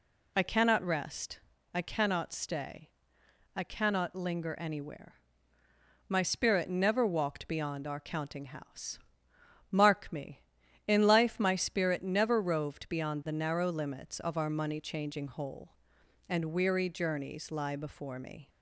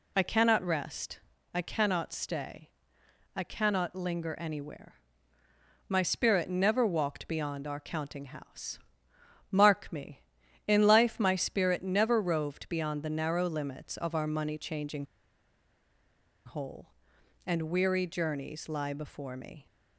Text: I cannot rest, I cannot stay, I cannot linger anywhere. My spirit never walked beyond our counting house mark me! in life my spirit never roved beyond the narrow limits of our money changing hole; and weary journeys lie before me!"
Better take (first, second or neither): first